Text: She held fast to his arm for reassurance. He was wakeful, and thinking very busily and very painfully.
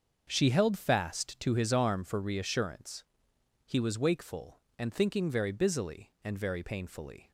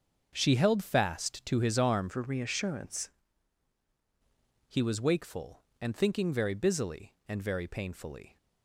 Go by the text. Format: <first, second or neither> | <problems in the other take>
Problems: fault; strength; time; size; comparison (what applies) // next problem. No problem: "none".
first | starts louder than the rest; until 1.3 s; 6.5 dB; also in the first // changes voice from "for" to "reassurance"; from 2.0 to 3.0 s; 1.0 s long